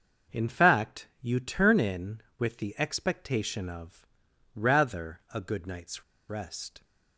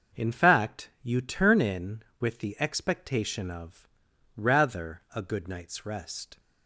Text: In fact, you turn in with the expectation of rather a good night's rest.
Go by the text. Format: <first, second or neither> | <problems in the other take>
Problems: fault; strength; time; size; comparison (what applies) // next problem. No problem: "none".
second | starts louder than the rest; noticeable; until 1.4 s; 6 dB; noticeable in the second // pauses between "of" and "rather"; noticeable; at 4.0 s; 0.48 s long; noticeable in the second // pauses between "night's" and "rest"; slight; at 6.0 s; 0.26 s long